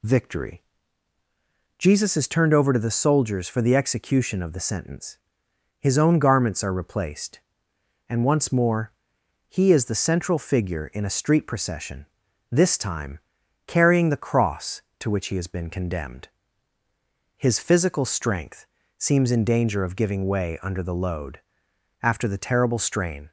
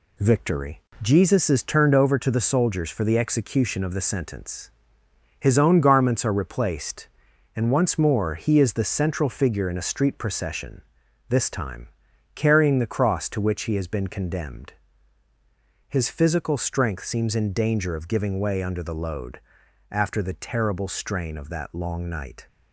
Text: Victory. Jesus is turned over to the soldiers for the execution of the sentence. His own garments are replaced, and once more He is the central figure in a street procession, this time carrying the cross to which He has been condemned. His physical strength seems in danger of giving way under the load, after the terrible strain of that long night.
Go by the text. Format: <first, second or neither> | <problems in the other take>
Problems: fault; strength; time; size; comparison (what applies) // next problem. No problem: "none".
second | pauses between "more" and "He"; noticeable; at 8.9 s; 0.56 s long // pauses between "time" and "carrying"; noticeable; at 13.1 s; 0.48 s long; also in the second // pauses between "strength" and "seems"; slight; at 18.6 s; 0.32 s long // stops before "of that long night"; at 23.2 s